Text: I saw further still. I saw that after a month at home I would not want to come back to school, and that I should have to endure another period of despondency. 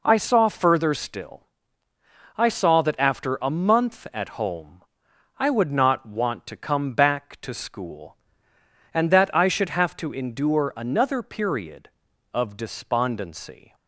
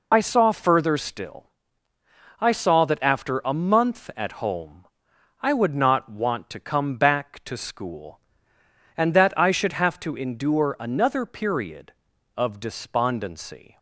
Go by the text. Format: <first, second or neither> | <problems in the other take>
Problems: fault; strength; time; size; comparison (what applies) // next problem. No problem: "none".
first | loses the start of "I"; at 0.1 s; 40 ms // pauses between "home" and "I"; noticeable; at 4.8 s; 0.56 s long; noticeable in the first